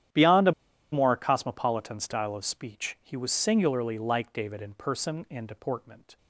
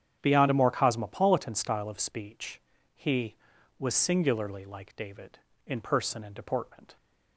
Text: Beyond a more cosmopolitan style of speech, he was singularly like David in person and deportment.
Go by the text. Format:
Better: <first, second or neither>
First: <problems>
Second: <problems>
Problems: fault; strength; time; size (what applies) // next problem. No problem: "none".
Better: second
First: starts louder than the rest; strong; until 1.5 s; 11 dB // pauses between "a" and "more"; at 0.5 s; 0.39 s long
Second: starts louder than the rest; strong; until 1.2 s; 9 dB